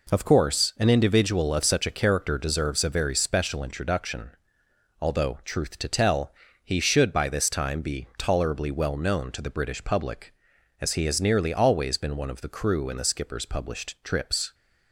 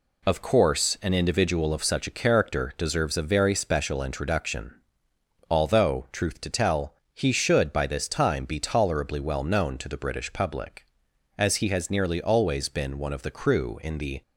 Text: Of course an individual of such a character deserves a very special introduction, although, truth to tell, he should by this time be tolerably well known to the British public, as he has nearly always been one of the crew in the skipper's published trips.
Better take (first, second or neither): first